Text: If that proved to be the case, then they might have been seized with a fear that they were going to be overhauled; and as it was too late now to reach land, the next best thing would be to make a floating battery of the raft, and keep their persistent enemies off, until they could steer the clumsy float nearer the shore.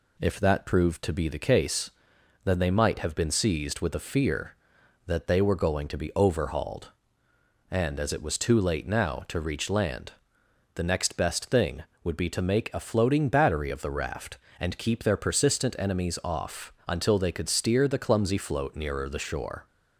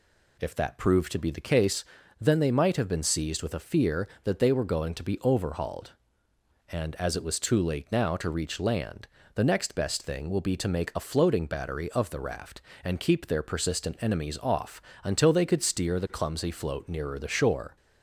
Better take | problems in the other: first | says "will" for "would"; at 10.2 s

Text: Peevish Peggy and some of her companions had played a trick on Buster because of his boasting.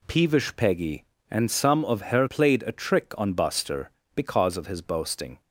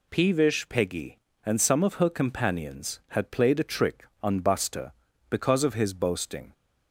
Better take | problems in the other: second | skips "companions had"; at 2.2 s

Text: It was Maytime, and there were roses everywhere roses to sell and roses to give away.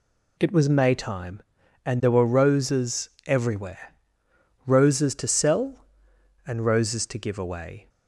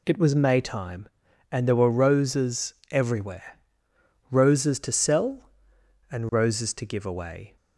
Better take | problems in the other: neither | pauses between "roses" and "everywhere"; slight; the same in both // pauses between "everywhere" and "roses"; noticeable; the same in both

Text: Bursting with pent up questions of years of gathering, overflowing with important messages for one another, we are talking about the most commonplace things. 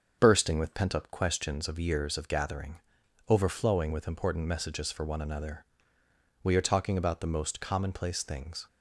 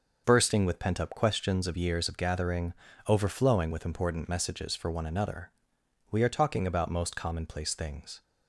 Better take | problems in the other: first | starts louder than the rest; noticeable; until 1.2 s; 6 dB; also in the first // skips "the"; at 6.9 s

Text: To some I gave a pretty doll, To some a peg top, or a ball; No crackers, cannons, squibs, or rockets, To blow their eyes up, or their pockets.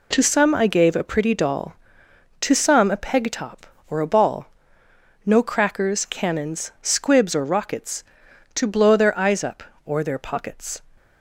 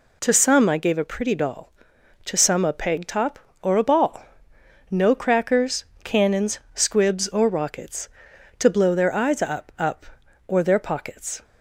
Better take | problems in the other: first | says "up" twice; at 9.7 s

